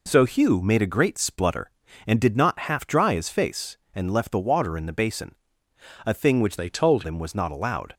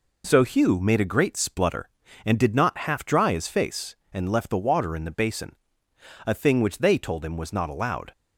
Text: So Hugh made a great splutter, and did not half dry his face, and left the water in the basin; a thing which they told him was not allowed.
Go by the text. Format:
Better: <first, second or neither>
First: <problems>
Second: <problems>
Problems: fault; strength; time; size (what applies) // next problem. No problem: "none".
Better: second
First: changes voice from "they" to "told"; from 6.5 to 7.0 s; 0.5 s long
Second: none